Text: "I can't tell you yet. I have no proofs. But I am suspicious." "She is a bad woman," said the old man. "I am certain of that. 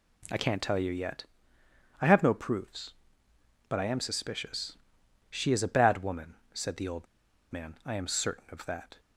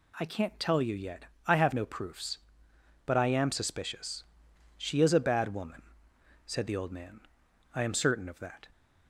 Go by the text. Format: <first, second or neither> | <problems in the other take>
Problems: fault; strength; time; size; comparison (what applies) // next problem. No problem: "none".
second | pauses between "old" and "man"; at 7.0 s; 0.45 s long